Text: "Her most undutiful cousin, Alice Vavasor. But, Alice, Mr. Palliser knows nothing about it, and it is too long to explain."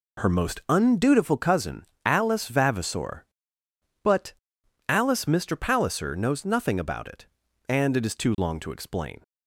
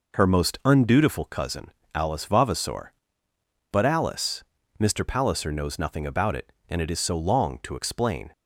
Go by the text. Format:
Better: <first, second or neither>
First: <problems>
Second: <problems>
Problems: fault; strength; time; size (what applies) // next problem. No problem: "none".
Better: first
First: none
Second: says "so" for "too"; at 6.9 s